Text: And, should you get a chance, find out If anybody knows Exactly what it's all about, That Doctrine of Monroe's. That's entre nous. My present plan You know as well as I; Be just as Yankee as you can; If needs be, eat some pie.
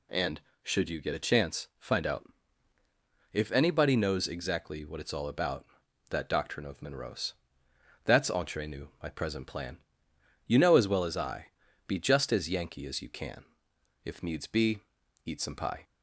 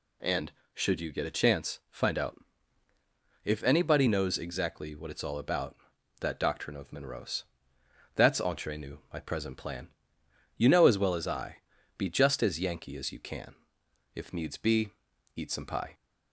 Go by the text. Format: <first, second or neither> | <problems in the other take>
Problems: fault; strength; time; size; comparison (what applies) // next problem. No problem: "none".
neither | pauses between "out" and "If"; the same in both // pauses between "plan" and "You"; noticeable; the same in both